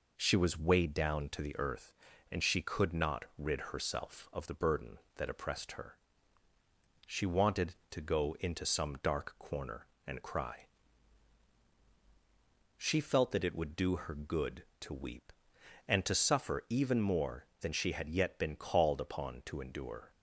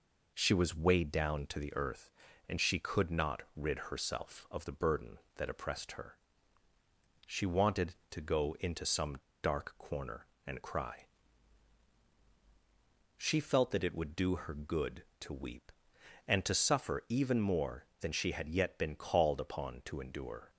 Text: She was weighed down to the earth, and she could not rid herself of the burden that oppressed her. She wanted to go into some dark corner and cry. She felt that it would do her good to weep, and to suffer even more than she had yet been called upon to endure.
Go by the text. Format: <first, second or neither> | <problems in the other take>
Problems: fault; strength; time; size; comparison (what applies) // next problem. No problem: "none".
first | pauses between "some" and "dark"; slight; at 9.1 s; 0.26 s long